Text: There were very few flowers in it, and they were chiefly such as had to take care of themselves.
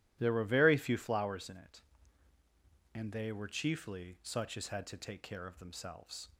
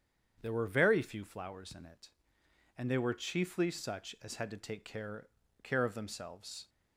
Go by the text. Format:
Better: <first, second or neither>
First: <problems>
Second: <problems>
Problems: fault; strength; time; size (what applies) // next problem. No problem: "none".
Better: first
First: none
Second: starts louder than the rest; strong; until 1.4 s; 8 dB // says "care" twice; at 5.6 s